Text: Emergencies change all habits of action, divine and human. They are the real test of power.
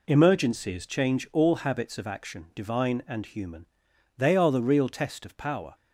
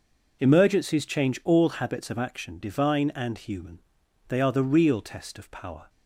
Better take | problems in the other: neither | none

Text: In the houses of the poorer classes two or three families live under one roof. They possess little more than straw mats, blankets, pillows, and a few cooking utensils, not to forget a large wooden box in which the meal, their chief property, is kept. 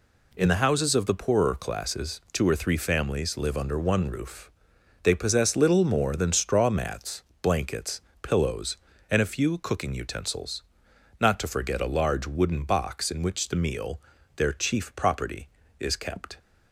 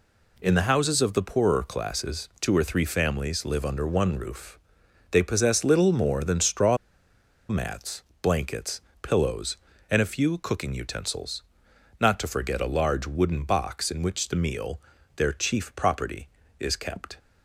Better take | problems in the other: first | pauses between "straw" and "mats"; noticeable; at 6.7 s; 0.72 s long

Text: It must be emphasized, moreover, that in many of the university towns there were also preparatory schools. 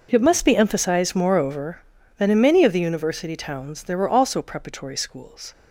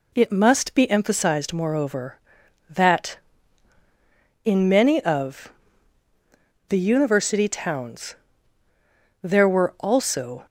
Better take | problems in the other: first | pauses between "of" and "the"; at 5.5 s; 1.1 s long // pauses between "towns" and "there"; at 8.1 s; 1.0 s long // stops before "preparatory schools"; at 10.4 s

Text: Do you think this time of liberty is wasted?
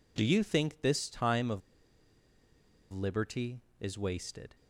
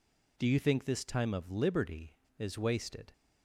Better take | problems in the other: second | pauses between "of" and "liberty"; strong; at 1.6 s; 1.3 s long

